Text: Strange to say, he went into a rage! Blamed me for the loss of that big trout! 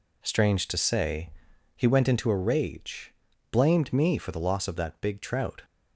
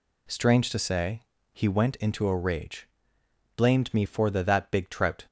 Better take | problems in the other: first | skips "loss of"; at 4.4 s

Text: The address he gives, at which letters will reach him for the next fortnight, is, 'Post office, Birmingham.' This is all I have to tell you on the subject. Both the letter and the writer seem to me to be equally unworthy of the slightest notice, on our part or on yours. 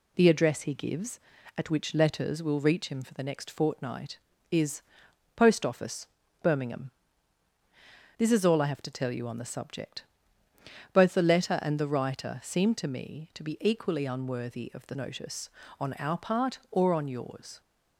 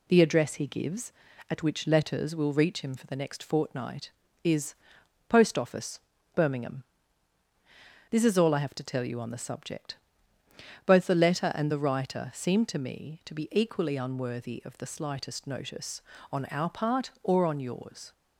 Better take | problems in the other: second | skips "slightest"; at 14.9 s

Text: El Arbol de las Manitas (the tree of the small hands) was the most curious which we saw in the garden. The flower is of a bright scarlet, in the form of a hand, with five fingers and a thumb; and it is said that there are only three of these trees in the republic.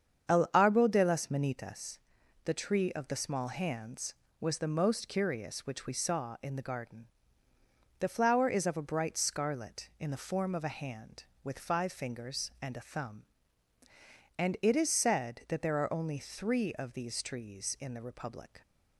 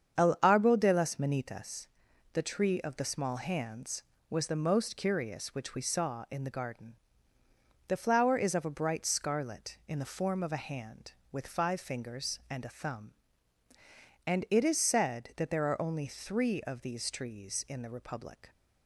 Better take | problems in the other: neither | starts louder than the rest; strong; the same in both

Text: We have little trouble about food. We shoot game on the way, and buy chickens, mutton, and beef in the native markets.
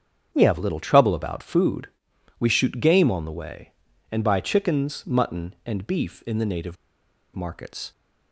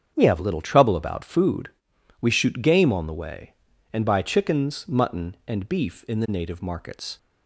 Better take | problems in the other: second | starts louder than the rest; strong; until 1.3 s; 7.5 dB; strong in the second // pauses between "native" and "markets"; noticeable; at 6.7 s; 0.59 s long

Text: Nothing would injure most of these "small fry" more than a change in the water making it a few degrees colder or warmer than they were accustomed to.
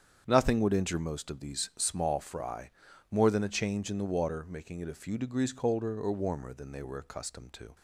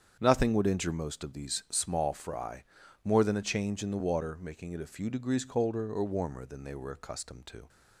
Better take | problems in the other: neither | starts louder than the rest; strong; the same in both // pauses between "fry" and "more"; the same in both

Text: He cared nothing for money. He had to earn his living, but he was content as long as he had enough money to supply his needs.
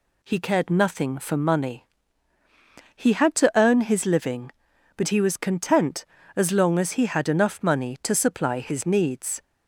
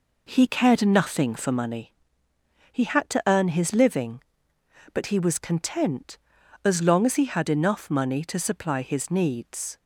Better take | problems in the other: first | starts louder than the rest; noticeable; until 1.7 s; 4.5 dB

